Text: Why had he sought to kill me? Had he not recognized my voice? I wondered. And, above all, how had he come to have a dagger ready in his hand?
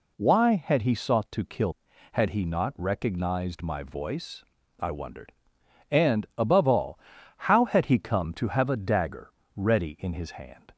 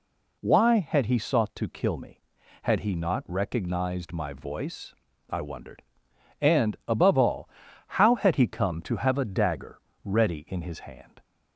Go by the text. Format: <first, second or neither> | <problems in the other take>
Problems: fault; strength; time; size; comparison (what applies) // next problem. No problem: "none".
second | skips "me"; at 1.9 s // pauses between "dagger" and "ready"; slight; at 9.2 s; 0.26 s long; slight in the second